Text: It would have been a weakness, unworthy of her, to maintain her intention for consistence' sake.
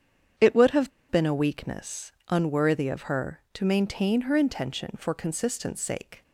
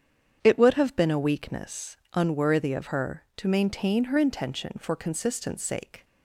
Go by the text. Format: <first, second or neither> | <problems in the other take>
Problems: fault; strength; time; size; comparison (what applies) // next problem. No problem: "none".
second | starts louder than the rest; strong; until 1.6 s; 8 dB; strong in the second // pauses between "have" and "been"; slight; at 0.9 s; 0.20 s long